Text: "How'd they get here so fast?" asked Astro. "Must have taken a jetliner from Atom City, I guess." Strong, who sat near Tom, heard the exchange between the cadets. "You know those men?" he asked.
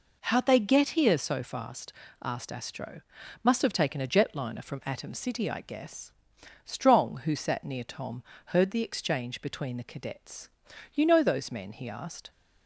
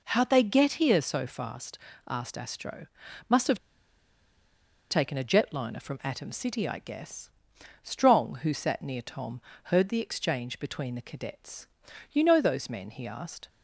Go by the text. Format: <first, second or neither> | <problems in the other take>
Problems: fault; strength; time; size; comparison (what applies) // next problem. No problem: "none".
first | pauses between "have" and "taken"; strong; at 3.5 s; 1.3 s long